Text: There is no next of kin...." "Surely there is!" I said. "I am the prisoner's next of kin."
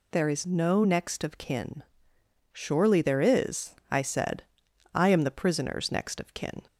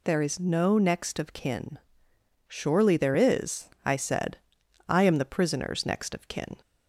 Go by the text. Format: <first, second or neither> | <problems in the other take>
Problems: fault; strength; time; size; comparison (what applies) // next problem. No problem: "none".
neither | none